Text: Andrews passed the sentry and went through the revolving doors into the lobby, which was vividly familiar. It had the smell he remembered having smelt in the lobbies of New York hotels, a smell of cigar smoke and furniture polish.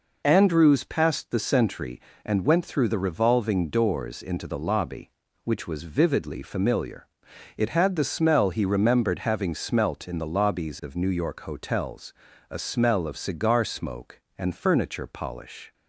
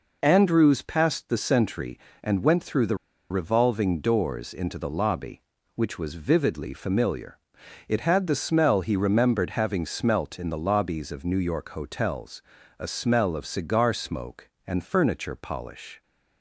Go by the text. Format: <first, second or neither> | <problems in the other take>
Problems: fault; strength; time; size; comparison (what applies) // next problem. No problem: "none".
first | pauses between "the" and "revolving"; slight; at 2.9 s; 0.33 s long